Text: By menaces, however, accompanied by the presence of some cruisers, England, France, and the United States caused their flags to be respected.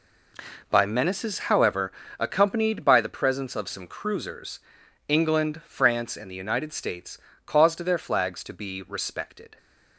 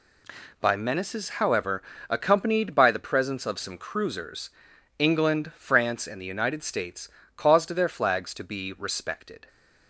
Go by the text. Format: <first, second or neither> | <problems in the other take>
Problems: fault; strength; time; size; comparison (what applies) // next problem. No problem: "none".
second | starts louder than the rest; noticeable; until 1.9 s; 4 dB // pauses between "States" and "caused"; slight; at 7.1 s; 0.28 s long; slight in the second